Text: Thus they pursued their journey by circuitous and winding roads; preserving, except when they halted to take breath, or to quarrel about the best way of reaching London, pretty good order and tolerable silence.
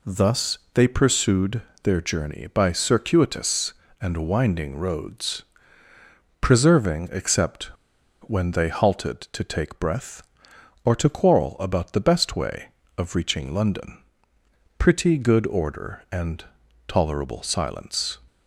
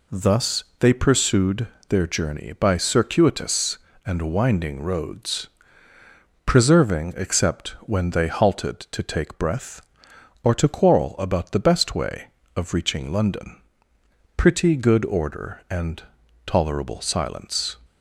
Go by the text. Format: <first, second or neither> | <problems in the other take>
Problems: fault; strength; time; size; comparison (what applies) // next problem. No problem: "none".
second | pauses between "pursued" and "their"; slight; at 1.6 s; 0.22 s long; slight in the second // pauses between "except" and "when"; noticeable; at 7.6 s; 0.57 s long // pauses between "and" and "tolerable"; at 16.4 s; 0.42 s long; also in the second